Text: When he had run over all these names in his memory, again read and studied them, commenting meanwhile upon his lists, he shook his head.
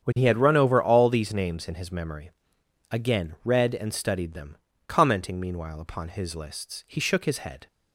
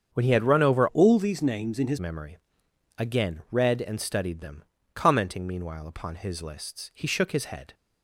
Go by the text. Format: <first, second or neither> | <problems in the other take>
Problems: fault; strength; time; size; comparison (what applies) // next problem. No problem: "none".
first | starts louder than the rest; strong; until 1.1 s; 7.5 dB; strong in the first // changes voice from "all" to "his"; from 0.8 to 1.9 s; 1.1 s long